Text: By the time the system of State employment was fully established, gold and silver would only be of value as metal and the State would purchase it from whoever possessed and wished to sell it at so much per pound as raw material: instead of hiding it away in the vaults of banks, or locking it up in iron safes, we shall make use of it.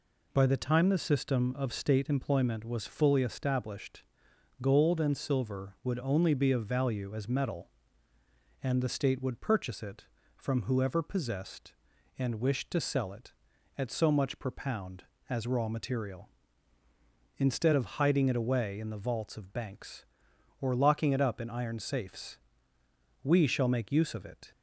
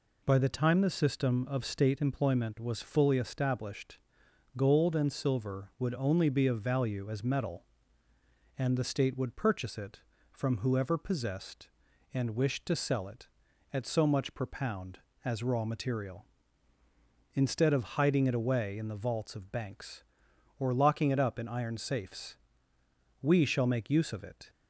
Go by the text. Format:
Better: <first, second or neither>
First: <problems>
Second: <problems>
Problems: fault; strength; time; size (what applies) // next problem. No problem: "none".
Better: neither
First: none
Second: none